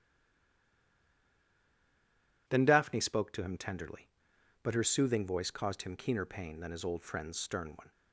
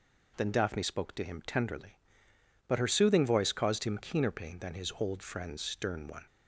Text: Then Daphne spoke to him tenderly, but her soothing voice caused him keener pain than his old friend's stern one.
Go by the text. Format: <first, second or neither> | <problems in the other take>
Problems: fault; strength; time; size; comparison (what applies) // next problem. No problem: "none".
second | stays silent before the first word; until 2.4 s; 2.4 s long